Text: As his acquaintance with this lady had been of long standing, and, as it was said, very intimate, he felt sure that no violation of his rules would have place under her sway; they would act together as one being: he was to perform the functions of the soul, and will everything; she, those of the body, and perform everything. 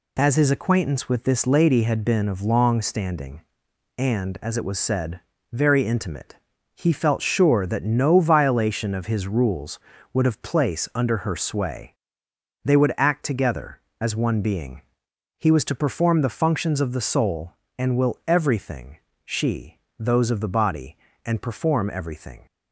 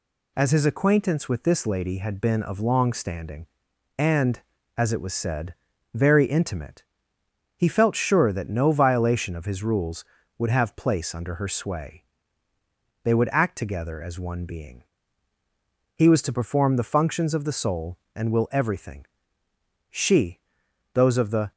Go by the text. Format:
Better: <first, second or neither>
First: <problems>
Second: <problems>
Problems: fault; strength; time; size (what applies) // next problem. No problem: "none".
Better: first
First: none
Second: stops before "body and perform everything"; at 21.5 s